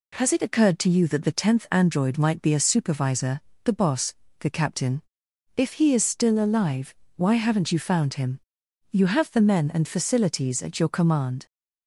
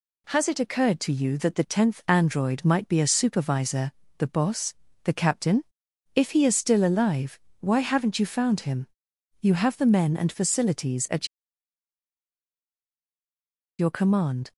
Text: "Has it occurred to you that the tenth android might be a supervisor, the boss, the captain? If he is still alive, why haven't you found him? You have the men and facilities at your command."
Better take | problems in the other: first | pauses between "at" and "your"; strong; at 11.2 s; 2.5 s long

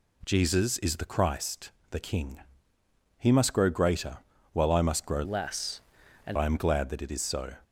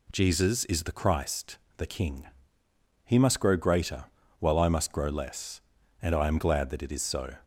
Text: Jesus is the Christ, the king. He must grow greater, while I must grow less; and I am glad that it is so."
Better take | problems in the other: second | changes voice from "less" to "and"; from 5.2 to 6.3 s; 1.1 s long

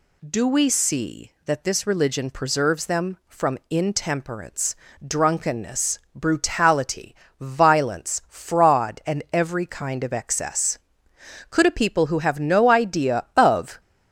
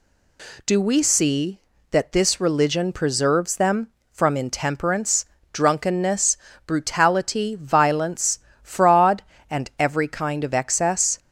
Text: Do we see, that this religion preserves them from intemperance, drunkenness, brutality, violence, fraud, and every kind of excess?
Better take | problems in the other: second | goes on to say "Could a people who have no idea of"; strong; from 11.5 s on; 2.2 s long

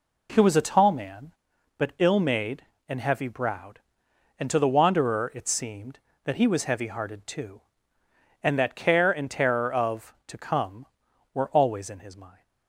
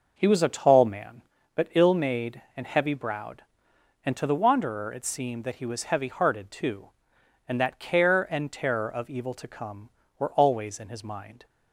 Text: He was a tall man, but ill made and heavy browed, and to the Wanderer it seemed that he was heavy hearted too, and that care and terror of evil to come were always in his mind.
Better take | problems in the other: second | skips "evil"; at 10.2 s

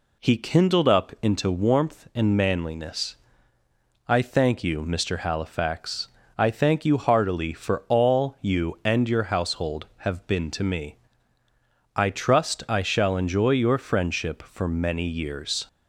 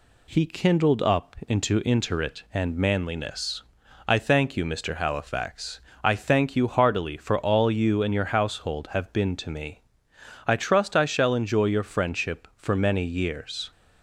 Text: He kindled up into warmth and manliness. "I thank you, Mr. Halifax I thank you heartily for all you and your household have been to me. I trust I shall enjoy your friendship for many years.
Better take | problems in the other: first | says "interit" for "warmth"; at 1.8 s // pauses between "Halifax" and "I"; slight; at 5.8 s; 0.22 s long; slight in the first

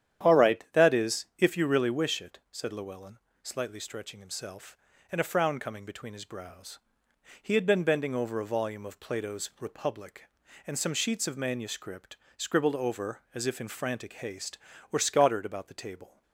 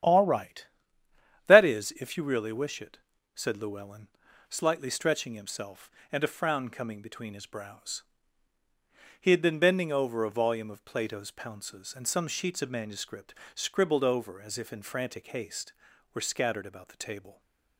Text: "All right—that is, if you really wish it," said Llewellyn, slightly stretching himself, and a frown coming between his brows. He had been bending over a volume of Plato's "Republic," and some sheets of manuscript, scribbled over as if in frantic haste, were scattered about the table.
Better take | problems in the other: first | starts louder than the rest; strong; until 1.8 s; 10 dB; strong in the first // says "Pounces" for "Republic"; at 11.2 s

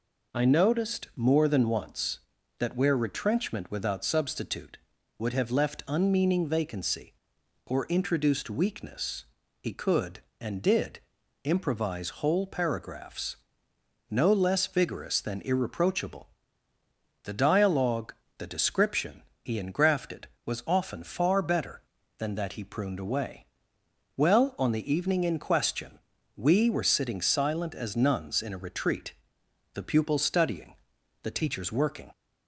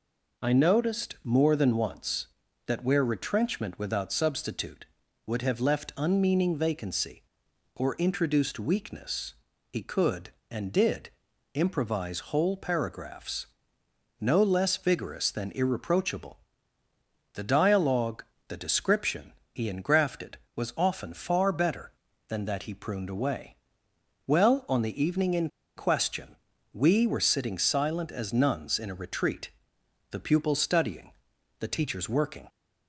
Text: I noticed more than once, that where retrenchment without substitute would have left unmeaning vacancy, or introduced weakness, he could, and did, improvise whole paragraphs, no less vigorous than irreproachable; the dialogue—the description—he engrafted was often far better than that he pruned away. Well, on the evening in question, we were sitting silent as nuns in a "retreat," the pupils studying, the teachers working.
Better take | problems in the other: first | pauses between "in" and "question"; slight; at 25.4 s; 0.27 s long

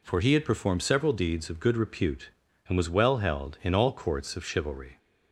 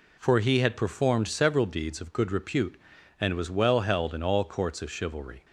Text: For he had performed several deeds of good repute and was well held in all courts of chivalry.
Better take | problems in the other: neither | none

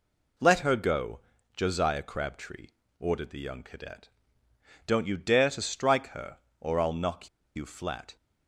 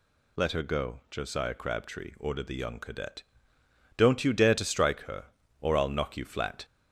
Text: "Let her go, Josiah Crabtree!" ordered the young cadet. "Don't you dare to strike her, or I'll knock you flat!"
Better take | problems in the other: second | pauses between "knock" and "you"; slight; at 7.2 s; 0.28 s long

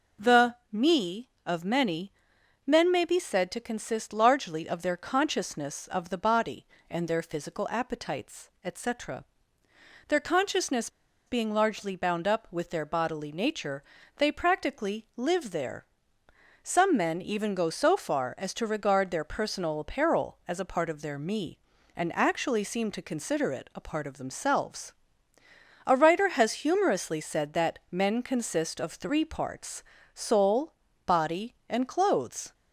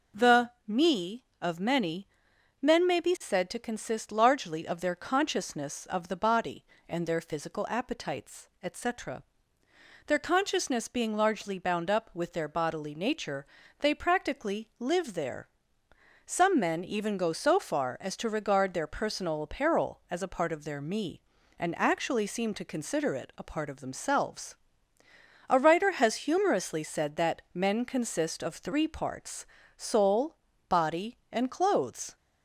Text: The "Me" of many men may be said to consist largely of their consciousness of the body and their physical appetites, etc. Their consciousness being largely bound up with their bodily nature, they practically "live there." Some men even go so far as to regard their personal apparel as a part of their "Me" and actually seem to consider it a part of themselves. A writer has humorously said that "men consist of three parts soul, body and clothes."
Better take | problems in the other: second | pauses between "many" and "men"; noticeable; at 2.1 s; 0.54 s long; noticeable in the second // pauses between "consciousness" and "being"; at 10.8 s; 0.36 s long // pauses between "parts" and "soul"; slight; at 29.8 s; 0.34 s long; slight in the second

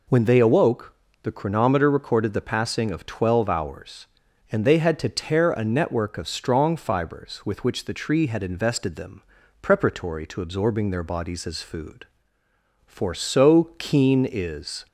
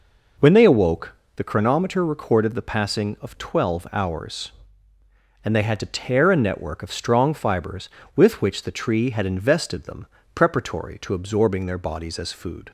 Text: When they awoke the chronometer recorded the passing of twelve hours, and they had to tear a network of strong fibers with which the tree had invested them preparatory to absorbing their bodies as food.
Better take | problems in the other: second | pauses between "awoke" and "the"; slight; at 0.9 s; 0.26 s long; slight in the second // pauses between "them" and "preparatory"; at 9.2 s; 0.40 s long; slight in the second // goes on to say "For so keen is"; strong; from 12.8 s on; 2.0 s long

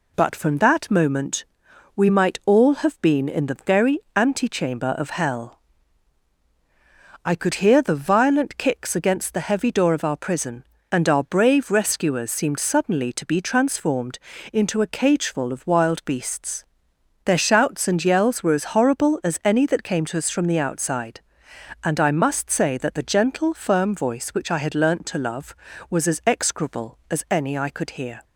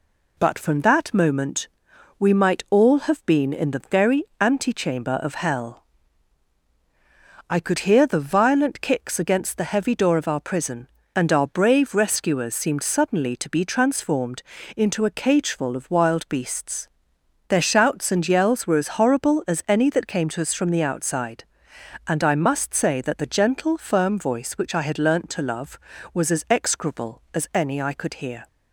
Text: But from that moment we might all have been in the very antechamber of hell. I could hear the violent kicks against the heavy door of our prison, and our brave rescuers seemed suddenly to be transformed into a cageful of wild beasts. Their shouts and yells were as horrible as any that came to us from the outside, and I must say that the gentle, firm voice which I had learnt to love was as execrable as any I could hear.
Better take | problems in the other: neither | pauses between "moment" and "we"; noticeable; the same in both // pauses between "very" and "antechamber"; slight; the same in both // pauses between "transformed" and "into"; slight; the same in both

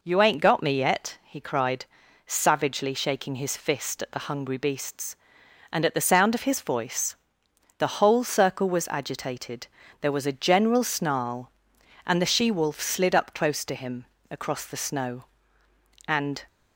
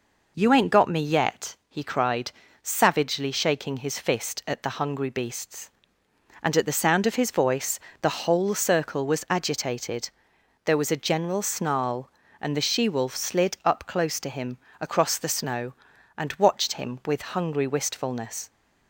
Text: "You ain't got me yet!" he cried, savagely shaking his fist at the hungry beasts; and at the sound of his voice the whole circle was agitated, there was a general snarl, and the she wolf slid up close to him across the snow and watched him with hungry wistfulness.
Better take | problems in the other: second | pauses between "voice" and "the"; noticeable; at 7.1 s; 0.62 s long; slight in the second // pauses between "him" and "across"; slight; at 14.0 s; 0.24 s long; slight in the second // stops before "watched him with hungry wistfulness"; at 16.4 s

